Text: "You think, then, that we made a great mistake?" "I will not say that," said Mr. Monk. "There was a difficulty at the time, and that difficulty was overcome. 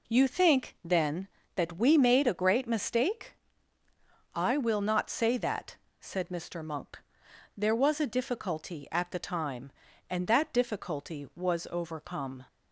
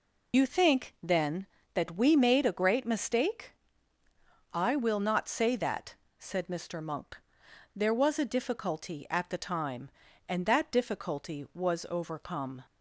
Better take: first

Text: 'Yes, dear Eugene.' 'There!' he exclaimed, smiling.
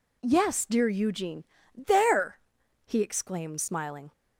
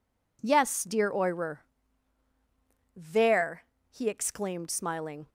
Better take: first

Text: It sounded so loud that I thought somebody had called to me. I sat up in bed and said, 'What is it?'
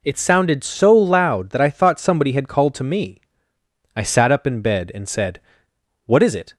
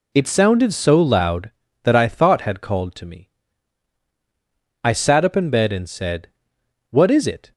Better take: first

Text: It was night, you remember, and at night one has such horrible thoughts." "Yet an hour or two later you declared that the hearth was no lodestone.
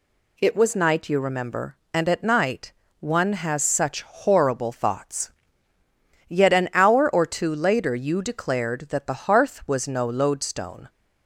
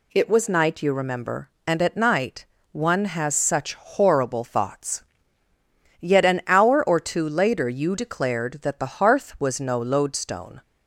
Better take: neither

